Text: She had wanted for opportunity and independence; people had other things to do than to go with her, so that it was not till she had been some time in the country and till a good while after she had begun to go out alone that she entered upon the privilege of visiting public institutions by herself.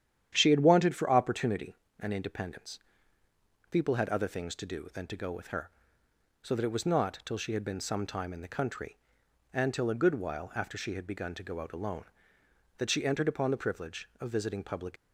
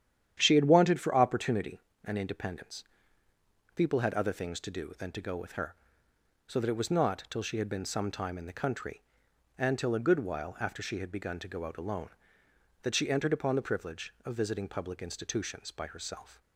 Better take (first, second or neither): second